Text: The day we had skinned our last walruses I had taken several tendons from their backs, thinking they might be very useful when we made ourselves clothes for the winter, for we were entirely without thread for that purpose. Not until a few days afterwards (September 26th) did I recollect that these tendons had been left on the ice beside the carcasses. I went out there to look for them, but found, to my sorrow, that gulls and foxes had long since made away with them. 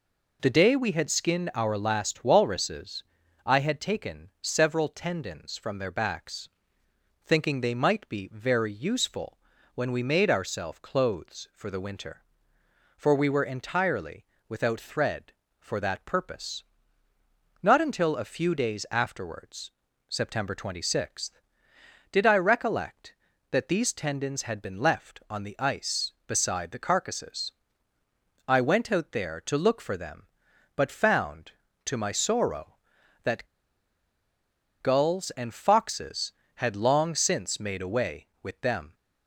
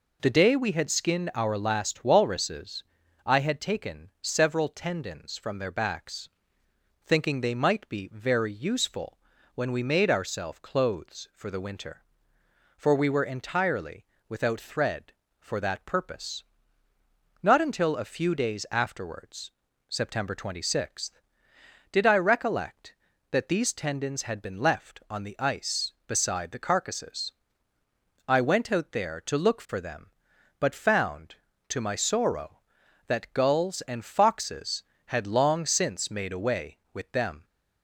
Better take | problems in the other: second | pauses between "walruses" and "I"; at 3.0 s; 0.42 s long; also in the second // pauses between "useful" and "when"; at 9.3 s; 0.38 s long; also in the second // pauses between "entirely" and "without"; slight; at 14.2 s; 0.24 s long; slight in the second // pauses between "that" and "gulls"; strong; at 33.4 s; 1.3 s long

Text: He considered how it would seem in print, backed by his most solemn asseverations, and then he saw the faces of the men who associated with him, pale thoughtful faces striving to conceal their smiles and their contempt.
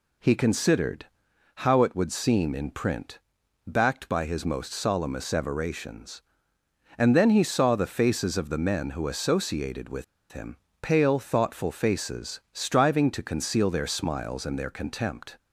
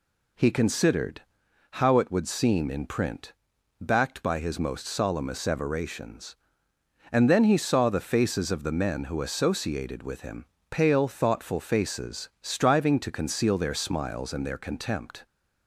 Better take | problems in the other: second | pauses between "considered" and "how"; noticeable; at 1.0 s; 0.60 s long; noticeable in the second // pauses between "with" and "him"; slight; at 10.0 s; 0.27 s long

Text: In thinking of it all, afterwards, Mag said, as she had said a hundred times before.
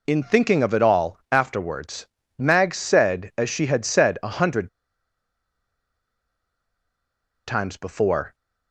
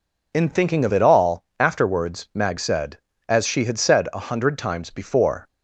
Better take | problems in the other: second | pauses between "hundred" and "times"; strong; at 4.6 s; 2.7 s long

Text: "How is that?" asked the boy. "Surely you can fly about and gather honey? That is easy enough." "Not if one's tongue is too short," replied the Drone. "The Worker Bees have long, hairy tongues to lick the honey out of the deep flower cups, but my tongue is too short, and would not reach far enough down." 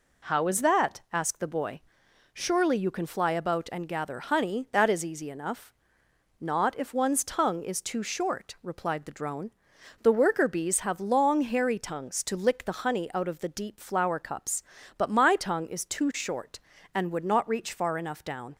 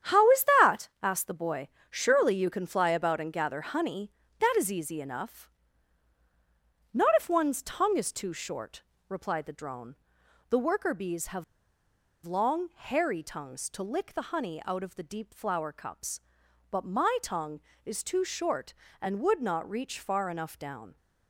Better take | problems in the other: first | starts louder than the rest; strong; until 1.3 s; 8 dB // pauses between "have" and "long"; noticeable; at 11.4 s; 0.81 s long

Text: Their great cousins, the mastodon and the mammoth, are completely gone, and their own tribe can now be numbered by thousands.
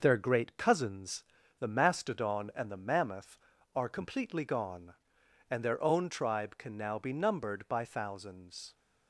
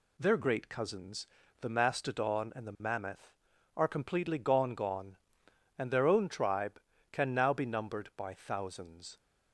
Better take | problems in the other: first | says "gone" twice; at 4.7 s

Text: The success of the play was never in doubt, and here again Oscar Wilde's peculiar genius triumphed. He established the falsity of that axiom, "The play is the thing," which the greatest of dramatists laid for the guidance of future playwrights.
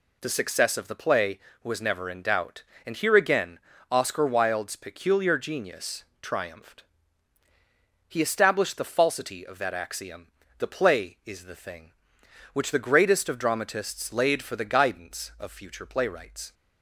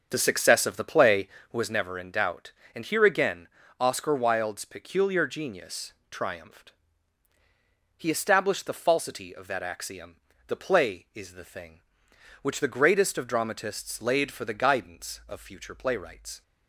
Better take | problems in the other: first | starts louder than the rest; strong; until 1.9 s; 7 dB // pauses between "again" and "Oscar"; slight; at 3.4 s; 0.32 s long; slight in the first // pauses between "genius" and "triumphed"; slight; at 5.9 s; 0.18 s long; slight in the first

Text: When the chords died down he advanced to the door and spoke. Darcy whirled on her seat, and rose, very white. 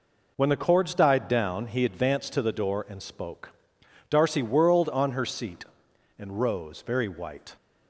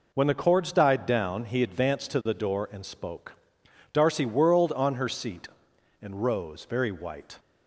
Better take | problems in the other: neither | none

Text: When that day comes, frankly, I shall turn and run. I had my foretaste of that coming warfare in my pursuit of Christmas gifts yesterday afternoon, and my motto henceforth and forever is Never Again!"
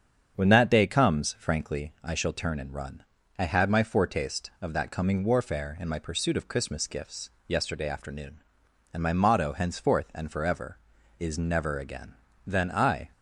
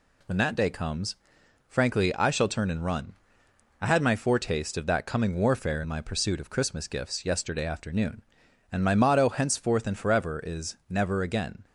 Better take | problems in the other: second | starts louder than the rest; strong; until 1.4 s; 7.5 dB // pauses between "gifts" and "yesterday"; slight; at 7.2 s; 0.16 s long // goes on to say "Then I"; noticeable; from 12.4 s on; 0.62 s long

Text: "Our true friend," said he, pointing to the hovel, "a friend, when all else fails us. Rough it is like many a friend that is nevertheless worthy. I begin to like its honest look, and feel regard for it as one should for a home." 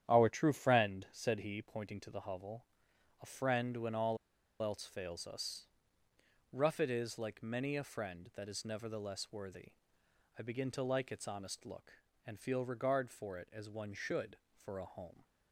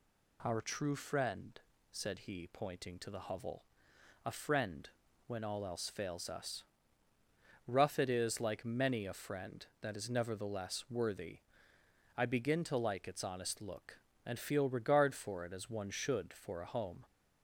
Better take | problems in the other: second | starts louder than the rest; strong; until 1.0 s; 10 dB // pauses between "all" and "else"; at 4.1 s; 0.45 s long

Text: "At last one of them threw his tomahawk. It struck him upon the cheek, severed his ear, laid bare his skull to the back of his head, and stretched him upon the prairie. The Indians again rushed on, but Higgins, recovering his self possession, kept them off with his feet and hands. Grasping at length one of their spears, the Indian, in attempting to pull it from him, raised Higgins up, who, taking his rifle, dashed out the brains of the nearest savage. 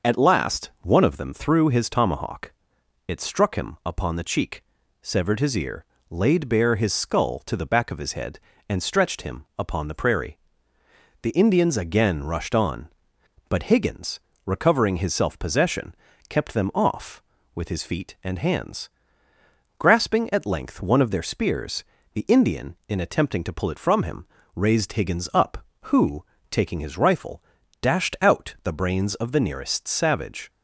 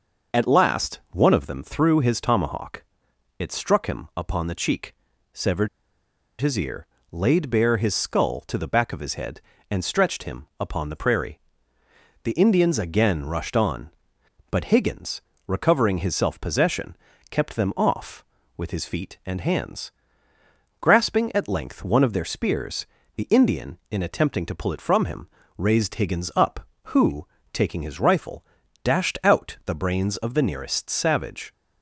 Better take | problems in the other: first | starts louder than the rest; noticeable; until 1.4 s; 6 dB; noticeable in the first // pauses between "severed" and "his"; noticeable; at 5.6 s; 0.73 s long

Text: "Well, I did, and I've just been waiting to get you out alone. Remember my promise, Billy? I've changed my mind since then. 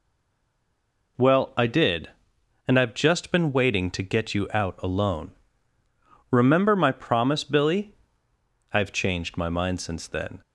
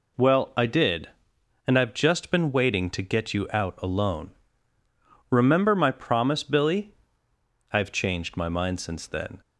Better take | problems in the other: second | stays silent before the first word; until 1.1 s; 1.1 s long

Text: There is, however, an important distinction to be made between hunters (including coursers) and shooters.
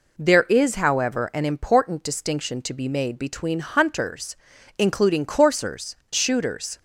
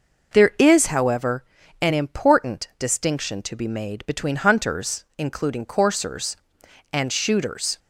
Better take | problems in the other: second | skips "and"; at 6.0 s

